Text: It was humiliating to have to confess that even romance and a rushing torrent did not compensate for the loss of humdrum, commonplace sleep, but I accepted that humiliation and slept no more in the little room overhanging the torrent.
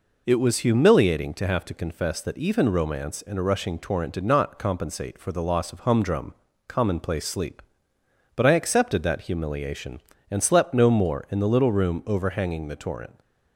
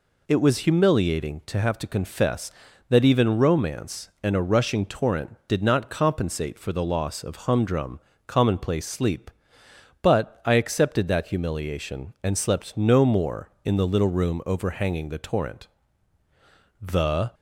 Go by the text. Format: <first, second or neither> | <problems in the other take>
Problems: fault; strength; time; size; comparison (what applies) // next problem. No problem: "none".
first | goes on to say "The"; from 16.7 s on; 0.54 s long